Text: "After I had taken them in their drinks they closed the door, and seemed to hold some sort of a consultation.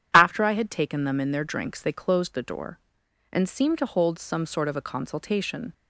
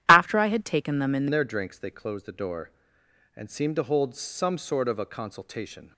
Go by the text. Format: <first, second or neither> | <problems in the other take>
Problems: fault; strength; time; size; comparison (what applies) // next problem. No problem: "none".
first | starts louder than the rest; strong; until 1.0 s; 12 dB; strong in the first // changes voice at "their"; from 1.3 s on; 4.6 s long